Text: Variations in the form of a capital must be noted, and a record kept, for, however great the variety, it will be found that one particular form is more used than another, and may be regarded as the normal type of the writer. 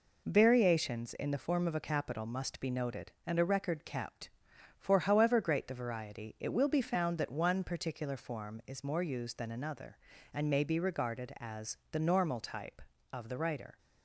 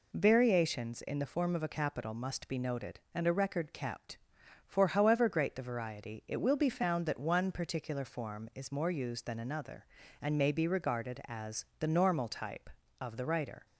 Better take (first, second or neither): second